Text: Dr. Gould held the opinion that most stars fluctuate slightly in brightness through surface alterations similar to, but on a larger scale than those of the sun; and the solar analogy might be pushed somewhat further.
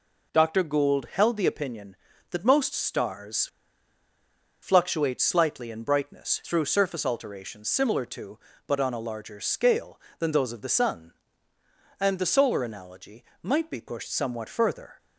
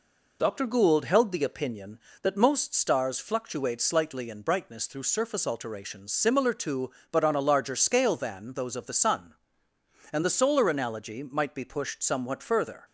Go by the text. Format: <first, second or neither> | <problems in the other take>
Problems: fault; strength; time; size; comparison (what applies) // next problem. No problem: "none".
second | pauses between "stars" and "fluctuate"; at 3.4 s; 1.1 s long // pauses between "analogy" and "might"; slight; at 13.2 s; 0.18 s long